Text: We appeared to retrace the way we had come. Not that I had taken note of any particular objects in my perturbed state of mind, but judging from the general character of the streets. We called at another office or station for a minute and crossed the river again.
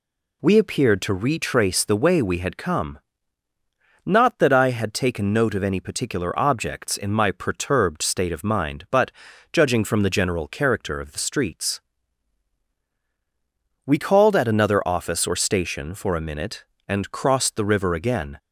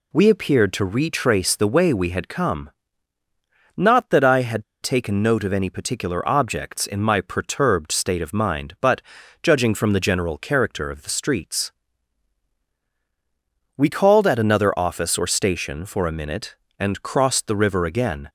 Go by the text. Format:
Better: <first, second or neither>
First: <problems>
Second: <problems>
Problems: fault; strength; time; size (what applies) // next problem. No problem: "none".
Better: first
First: pauses between "but" and "judging"; at 9.1 s; 0.40 s long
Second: pauses between "had" and "taken"; slight; at 4.6 s; 0.19 s long // pauses between "but" and "judging"; at 9.0 s; 0.40 s long